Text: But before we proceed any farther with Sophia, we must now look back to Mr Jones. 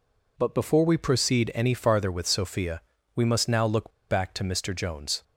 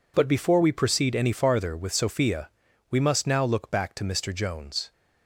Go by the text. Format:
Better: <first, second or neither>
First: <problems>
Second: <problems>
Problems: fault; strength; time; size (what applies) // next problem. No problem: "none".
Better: second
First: pauses between "look" and "back"; slight; at 3.9 s; 0.17 s long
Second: none